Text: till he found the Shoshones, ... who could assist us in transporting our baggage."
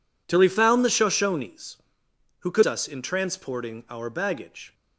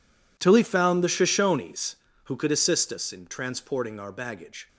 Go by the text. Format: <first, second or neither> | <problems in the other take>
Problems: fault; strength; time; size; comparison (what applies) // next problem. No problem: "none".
second | skips "assist"; at 2.6 s